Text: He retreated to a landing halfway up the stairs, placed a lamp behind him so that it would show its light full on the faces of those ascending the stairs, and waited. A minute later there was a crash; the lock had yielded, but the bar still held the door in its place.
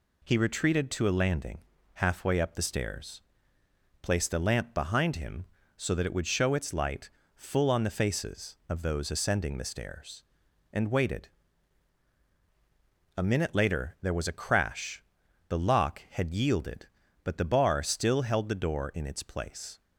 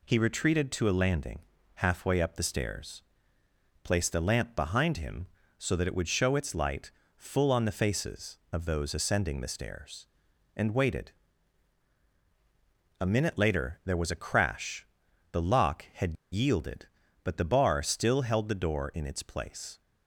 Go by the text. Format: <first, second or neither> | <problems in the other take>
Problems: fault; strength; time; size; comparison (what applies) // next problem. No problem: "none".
first | pauses between "landing" and "halfway"; slight; at 1.3 s; 0.36 s long; slight in the first // pauses between "light" and "full"; slight; at 6.9 s; 0.24 s long; slight in the first // pauses between "had" and "yielded"; slight; at 16.1 s; 0.19 s long